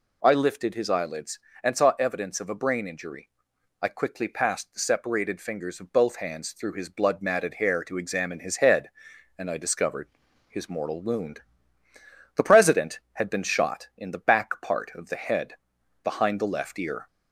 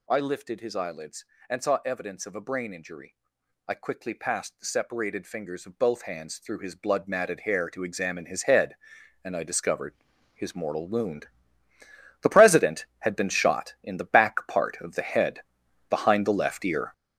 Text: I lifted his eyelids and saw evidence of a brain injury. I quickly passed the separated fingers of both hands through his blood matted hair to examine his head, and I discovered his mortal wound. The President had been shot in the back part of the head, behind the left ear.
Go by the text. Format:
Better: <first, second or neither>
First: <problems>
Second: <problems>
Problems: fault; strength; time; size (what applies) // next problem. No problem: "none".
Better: first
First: pauses between "discovered" and "his"; at 10.0 s; 0.38 s long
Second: gets louder; strong; throughout; 9.5 dB // pauses between "discovered" and "his"; at 9.9 s; 0.38 s long